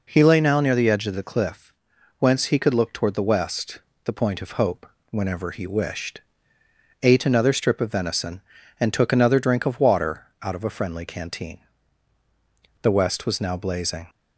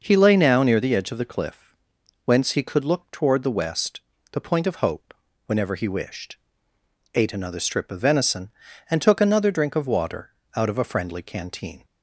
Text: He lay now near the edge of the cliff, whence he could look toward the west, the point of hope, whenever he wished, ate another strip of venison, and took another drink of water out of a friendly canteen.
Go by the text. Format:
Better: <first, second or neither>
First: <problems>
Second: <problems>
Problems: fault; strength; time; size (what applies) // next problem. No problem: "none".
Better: second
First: pauses between "water" and "out"; slight; at 10.2 s; 0.18 s long // goes on to say "The west was now blazing"; noticeable; from 12.8 s on; 1.2 s long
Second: pauses between "water" and "out"; slight; at 10.3 s; 0.26 s long